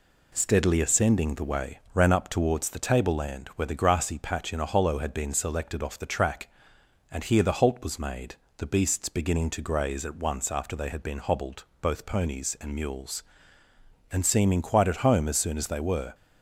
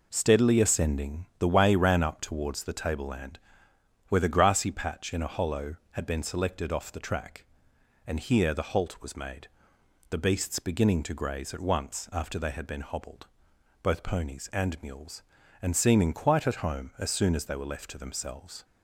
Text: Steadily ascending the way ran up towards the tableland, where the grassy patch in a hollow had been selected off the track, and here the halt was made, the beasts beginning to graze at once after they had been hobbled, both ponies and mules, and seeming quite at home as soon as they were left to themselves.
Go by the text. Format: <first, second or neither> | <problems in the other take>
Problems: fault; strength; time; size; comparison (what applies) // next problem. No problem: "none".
second | pauses between "way" and "ran"; slight; at 1.7 s; 0.16 s long // stops before "left to themselves"; at 16.1 s